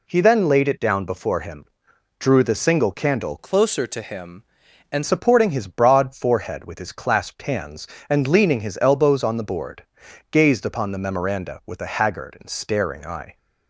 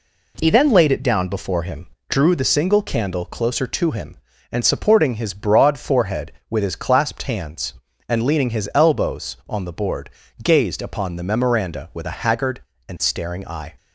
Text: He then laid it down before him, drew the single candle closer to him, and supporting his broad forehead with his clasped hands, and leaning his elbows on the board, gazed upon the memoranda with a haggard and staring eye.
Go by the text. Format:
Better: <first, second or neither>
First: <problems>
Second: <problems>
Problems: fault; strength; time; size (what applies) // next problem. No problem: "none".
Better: second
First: changes voice from "closer" to "and"; from 3.3 to 5.0 s; 1.7 s long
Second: none